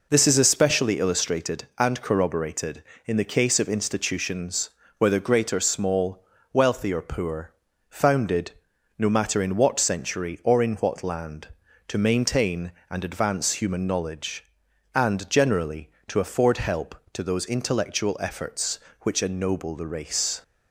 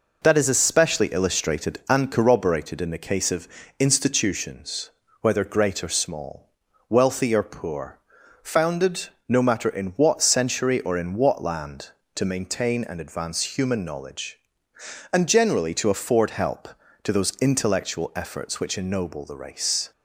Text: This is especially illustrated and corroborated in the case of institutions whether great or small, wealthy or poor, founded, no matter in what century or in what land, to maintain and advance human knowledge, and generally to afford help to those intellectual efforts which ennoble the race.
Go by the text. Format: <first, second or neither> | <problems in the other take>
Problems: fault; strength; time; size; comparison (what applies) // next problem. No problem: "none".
first | says "That" for "This"; at 0.2 s // pauses between "of" and "institutions"; slight; at 3.4 s; 0.32 s long // pauses between "institutions" and "whether"; slight; at 4.8 s; 0.32 s long; slight in the first